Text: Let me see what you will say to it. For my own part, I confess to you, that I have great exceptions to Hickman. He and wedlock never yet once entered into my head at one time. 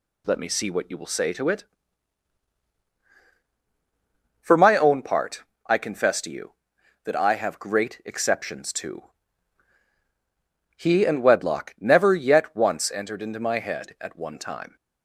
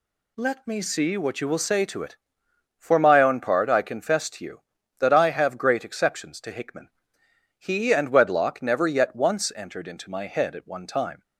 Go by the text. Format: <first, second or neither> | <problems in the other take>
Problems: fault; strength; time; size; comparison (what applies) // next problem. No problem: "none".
second | skips "Hickman"; at 9.8 s